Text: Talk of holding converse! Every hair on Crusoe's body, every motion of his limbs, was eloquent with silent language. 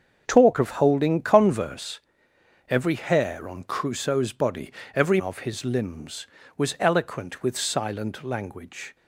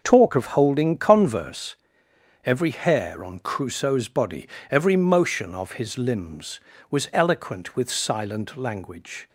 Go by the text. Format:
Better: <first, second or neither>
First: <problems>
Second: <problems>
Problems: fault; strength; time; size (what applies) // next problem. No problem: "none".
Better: second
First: starts louder than the rest; until 1.2 s; 6.5 dB // skips "motion"; at 5.2 s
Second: starts louder than the rest; noticeable; until 1.0 s; 6 dB